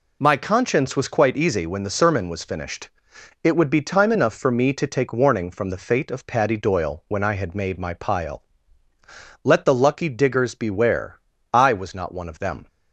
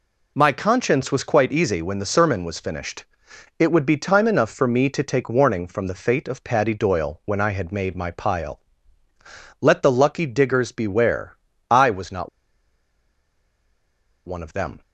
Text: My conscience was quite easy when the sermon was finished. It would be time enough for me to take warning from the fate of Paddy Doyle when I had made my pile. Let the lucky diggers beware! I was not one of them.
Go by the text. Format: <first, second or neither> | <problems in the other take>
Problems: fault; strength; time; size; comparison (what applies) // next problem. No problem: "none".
first | pauses between "not" and "one"; strong; at 12.2 s; 1.9 s long